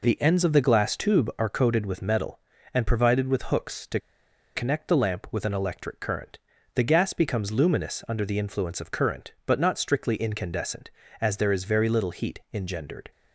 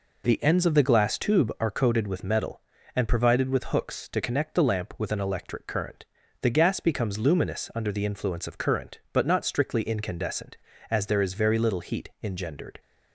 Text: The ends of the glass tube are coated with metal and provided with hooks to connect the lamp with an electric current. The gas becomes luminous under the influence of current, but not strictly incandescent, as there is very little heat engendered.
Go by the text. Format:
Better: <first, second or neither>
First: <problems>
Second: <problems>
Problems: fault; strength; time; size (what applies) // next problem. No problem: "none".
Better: second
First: pauses between "to" and "connect"; noticeable; at 3.9 s; 0.57 s long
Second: none